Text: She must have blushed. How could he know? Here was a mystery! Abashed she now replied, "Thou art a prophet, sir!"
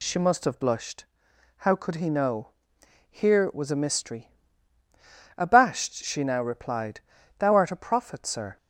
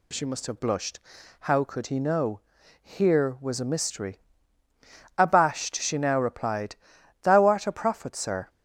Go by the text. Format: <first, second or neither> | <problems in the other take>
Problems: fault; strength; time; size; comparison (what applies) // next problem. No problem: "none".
neither | none